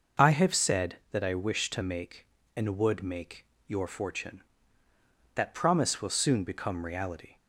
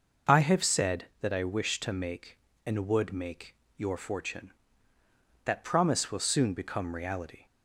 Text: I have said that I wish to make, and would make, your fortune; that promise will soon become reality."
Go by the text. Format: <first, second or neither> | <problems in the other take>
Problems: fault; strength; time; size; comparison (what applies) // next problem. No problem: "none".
neither | none